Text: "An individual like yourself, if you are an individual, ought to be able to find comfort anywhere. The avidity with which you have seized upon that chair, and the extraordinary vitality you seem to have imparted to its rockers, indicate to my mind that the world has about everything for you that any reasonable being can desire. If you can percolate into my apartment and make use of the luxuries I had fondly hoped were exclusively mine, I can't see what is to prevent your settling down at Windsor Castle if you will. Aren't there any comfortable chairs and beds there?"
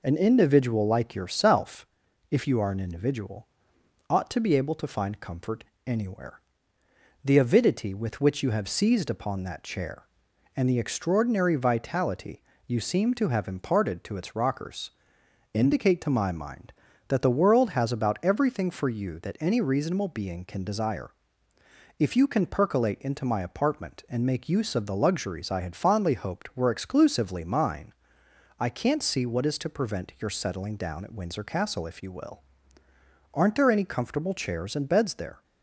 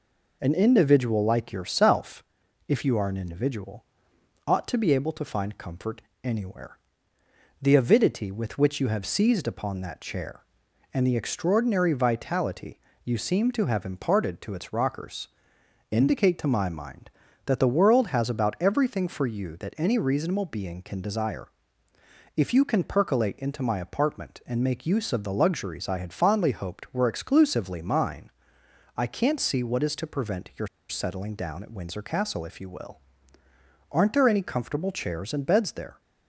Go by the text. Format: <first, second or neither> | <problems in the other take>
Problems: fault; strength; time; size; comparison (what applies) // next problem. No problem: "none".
first | pauses between "comfort" and "anywhere"; slight; at 6.0 s; 0.22 s long; slight in the first // pauses between "vitality" and "you"; slight; at 12.7 s; 0.24 s long; slight in the first // pauses between "your" and "settling"; slight; at 30.6 s; 0.21 s long